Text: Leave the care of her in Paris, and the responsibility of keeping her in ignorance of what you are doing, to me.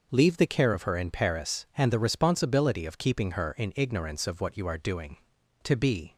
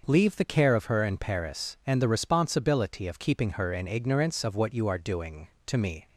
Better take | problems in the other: second | says "be" for "me"; at 5.7 s

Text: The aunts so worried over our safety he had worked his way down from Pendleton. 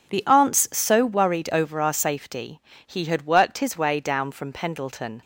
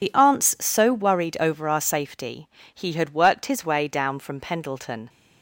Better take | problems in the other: first | loses the start of "The"; at 0.0 s; 50 ms // pauses between "safety" and "he"; slight; at 2.4 s; 0.26 s long; slight in the first

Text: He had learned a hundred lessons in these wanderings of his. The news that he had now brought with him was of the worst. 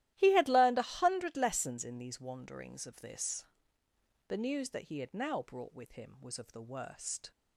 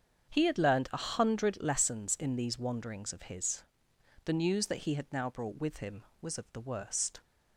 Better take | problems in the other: second | starts louder than the rest; strong; until 1.1 s; 14 dB; strong in the second // says "this" for "his"; at 3.0 s

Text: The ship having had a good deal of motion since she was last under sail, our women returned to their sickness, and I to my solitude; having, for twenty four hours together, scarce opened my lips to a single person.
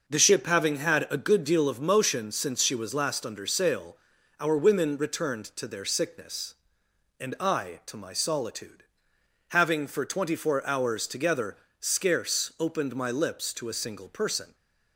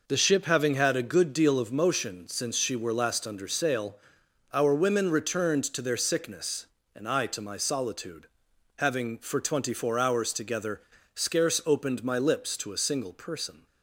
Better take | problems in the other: first | says "were" for "was"; at 2.7 s

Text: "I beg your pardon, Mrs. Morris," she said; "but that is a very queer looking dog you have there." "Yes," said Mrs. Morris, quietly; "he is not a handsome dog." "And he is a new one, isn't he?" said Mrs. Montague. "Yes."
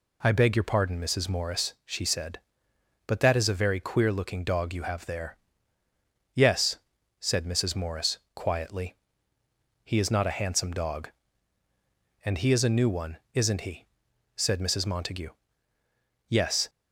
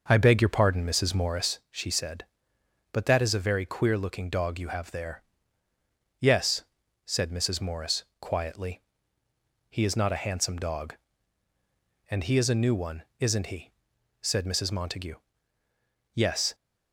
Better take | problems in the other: first | starts louder than the rest; noticeable; until 1.6 s; 5.5 dB

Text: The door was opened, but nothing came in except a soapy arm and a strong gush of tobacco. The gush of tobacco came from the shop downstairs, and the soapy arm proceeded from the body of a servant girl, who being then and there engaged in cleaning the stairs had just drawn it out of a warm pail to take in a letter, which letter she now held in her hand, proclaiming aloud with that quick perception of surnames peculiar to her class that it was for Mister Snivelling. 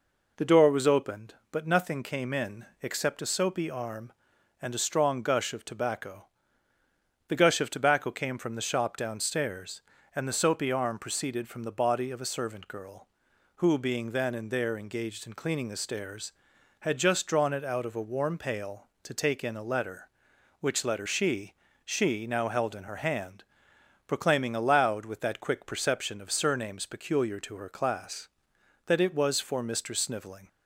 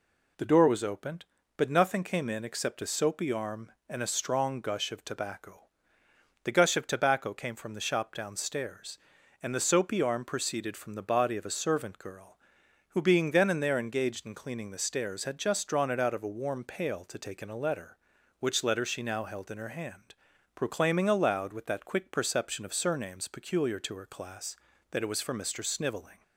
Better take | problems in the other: second | pauses between "in" and "except"; slight; at 2.6 s; 0.16 s long // says "she" twice; at 21.8 s

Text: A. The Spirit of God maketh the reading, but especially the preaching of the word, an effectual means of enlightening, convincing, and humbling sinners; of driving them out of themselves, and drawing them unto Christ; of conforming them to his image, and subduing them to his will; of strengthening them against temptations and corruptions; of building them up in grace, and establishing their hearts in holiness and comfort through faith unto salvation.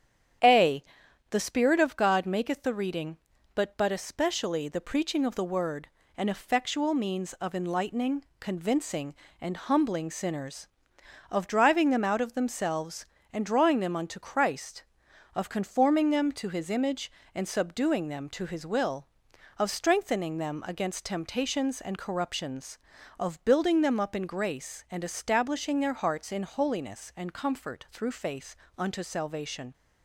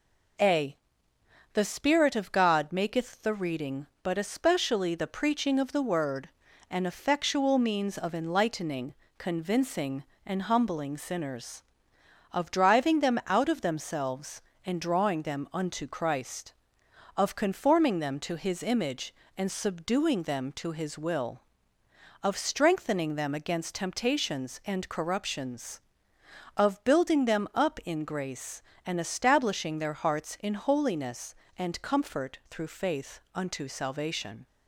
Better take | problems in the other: second | starts louder than the rest; strong; until 1.9 s; 9 dB // says "but" twice; at 3.7 s // pauses between "faith" and "unto"; slight; at 28.5 s; 0.22 s long

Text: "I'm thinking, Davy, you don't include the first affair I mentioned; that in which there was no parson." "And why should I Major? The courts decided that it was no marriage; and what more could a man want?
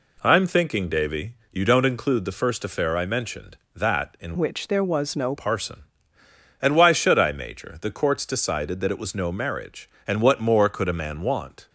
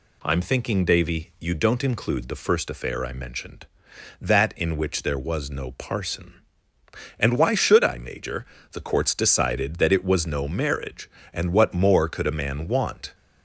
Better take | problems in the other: second | changes voice from "which" to "no"; from 4.3 to 5.3 s; 1.0 s long

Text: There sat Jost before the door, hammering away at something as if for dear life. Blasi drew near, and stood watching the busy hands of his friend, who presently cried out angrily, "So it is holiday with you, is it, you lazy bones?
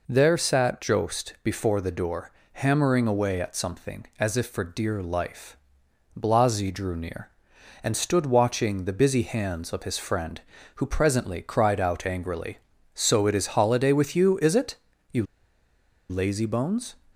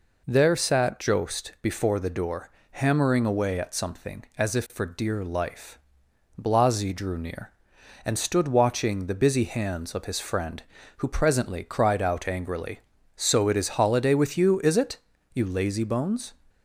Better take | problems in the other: second | pauses between "you" and "lazy"; noticeable; at 15.2 s; 0.86 s long

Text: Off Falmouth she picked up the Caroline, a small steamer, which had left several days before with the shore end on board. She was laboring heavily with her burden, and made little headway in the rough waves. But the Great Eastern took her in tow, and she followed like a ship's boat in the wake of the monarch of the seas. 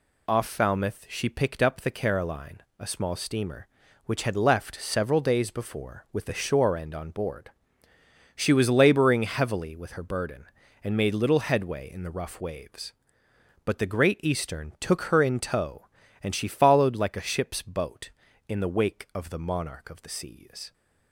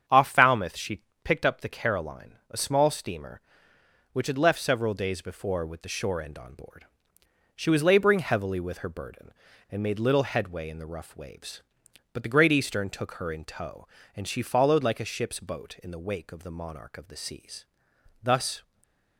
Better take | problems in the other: first | starts louder than the rest; strong; until 1.3 s; 7.5 dB // pauses between "she" and "picked"; slight; at 1.0 s; 0.22 s long // goes on to say "Thus"; slight; from 18.2 s on; 0.40 s long // stays silent after the last word; slight; from 18.6 s on; 0.5 s long

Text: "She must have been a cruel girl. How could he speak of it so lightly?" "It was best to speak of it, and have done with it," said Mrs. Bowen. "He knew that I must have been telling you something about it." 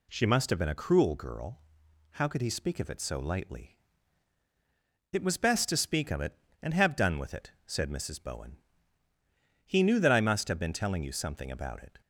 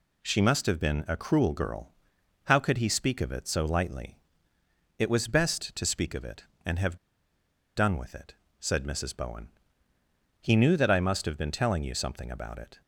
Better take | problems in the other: first | pauses between "have" and "done"; noticeable; at 6.9 s; 0.79 s long

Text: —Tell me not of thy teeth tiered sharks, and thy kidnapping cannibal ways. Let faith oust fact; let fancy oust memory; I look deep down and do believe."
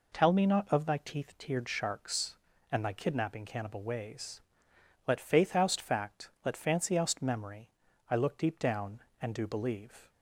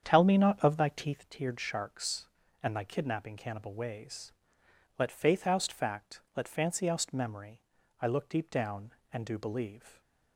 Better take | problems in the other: first | starts louder than the rest; strong; until 1.2 s; 8 dB

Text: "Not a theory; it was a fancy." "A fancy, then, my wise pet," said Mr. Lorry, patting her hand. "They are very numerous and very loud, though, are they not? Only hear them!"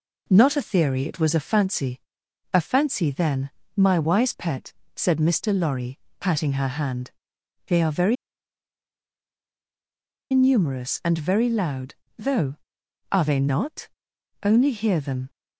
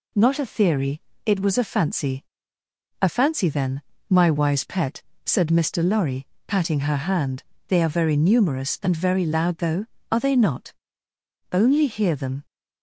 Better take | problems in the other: second | pauses between "very" and "numerous"; strong; at 8.1 s; 2.1 s long

